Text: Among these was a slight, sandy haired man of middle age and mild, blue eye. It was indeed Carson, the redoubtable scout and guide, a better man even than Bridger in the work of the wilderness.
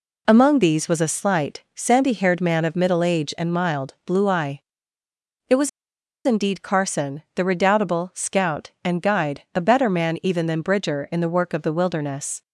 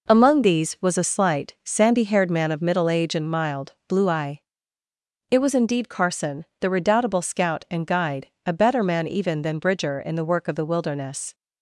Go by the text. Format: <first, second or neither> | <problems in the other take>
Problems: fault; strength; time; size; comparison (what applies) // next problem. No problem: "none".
second | pauses between "was" and "indeed"; noticeable; at 5.6 s; 0.55 s long